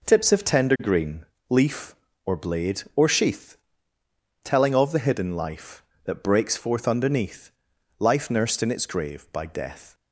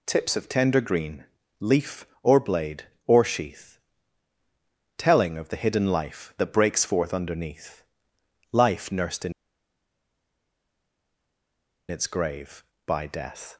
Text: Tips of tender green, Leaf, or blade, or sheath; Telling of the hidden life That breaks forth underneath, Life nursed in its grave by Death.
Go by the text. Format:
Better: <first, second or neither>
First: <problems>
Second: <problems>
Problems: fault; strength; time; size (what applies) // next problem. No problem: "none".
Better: first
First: none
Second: pauses between "in" and "its"; strong; at 9.3 s; 2.5 s long